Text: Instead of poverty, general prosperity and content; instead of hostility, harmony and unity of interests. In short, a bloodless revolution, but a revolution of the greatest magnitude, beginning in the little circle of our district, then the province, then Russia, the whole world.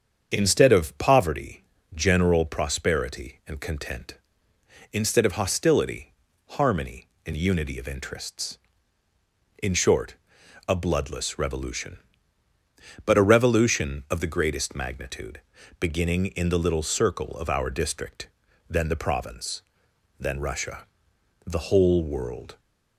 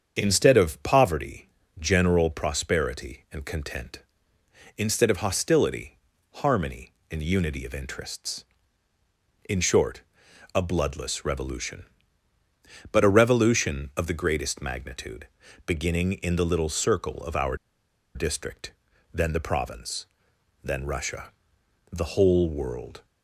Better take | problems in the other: first | starts louder than the rest; strong; until 1.2 s; 7.5 dB; strong in the first // pauses between "our" and "district"; noticeable; at 17.5 s; 0.59 s long

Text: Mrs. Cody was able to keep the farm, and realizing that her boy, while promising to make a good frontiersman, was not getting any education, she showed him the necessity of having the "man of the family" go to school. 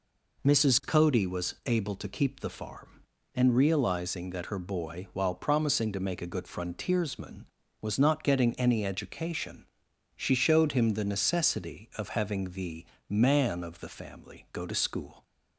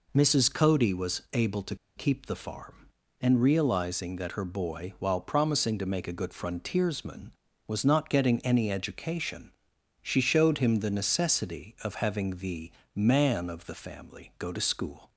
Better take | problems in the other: first | pauses between "to" and "keep"; slight; at 1.7 s; 0.20 s long // pauses between "the" and "man"; slight; at 12.7 s; 0.24 s long; slight in the first

